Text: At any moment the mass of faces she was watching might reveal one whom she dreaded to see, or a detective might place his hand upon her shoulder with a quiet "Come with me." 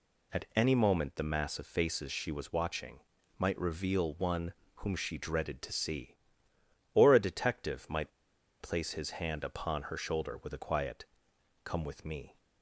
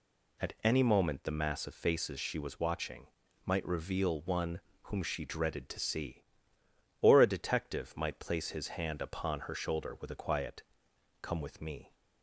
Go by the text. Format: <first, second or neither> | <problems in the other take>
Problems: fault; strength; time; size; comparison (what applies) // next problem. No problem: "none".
second | pauses between "watching" and "might"; at 2.9 s; 0.38 s long; also in the second // pauses between "one" and "whom"; slight; at 4.5 s; 0.22 s long; slight in the second // pauses between "might" and "place"; noticeable; at 8.1 s; 0.51 s long // pauses between "quiet" and "Come"; noticeable; at 11.0 s; 0.62 s long; noticeable in the second